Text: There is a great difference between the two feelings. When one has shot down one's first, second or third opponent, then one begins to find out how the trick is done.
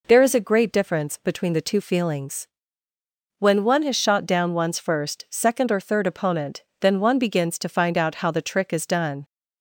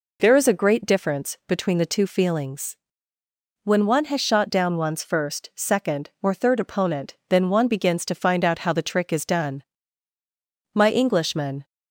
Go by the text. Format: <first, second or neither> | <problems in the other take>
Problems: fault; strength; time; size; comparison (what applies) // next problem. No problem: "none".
first | goes on to say "My Englishman"; noticeable; from 10.7 s on; 0.90 s long